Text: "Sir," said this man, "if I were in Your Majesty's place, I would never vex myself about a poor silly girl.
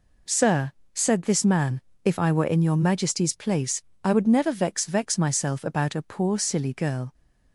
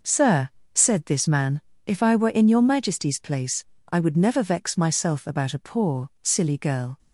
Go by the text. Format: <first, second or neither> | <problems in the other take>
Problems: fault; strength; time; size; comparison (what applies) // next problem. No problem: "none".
second | says "vex" twice; at 4.8 s